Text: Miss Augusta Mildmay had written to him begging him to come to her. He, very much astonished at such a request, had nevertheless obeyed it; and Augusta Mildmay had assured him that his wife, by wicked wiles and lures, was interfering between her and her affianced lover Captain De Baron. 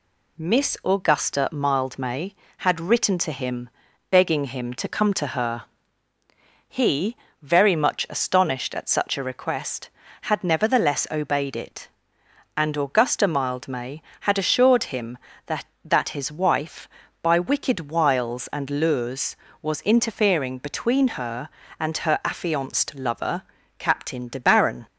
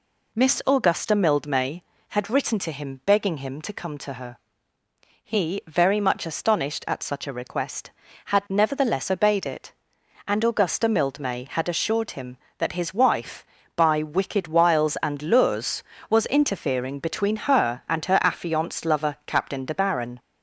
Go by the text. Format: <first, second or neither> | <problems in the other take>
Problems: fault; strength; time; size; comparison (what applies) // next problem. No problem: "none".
second | pauses between "him" and "begging"; at 3.7 s; 0.40 s long // says "that" twice; at 15.8 s // pauses between "lover" and "Captain"; slight; at 23.4 s; 0.34 s long